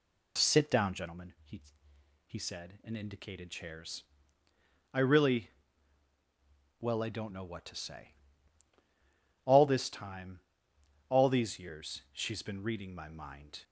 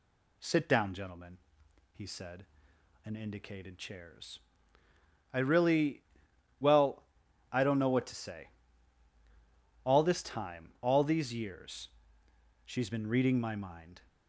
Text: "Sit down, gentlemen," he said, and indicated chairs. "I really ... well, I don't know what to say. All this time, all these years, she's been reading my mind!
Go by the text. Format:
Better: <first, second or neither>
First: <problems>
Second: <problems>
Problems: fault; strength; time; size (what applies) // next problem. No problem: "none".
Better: second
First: says "he" twice; at 2.2 s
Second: none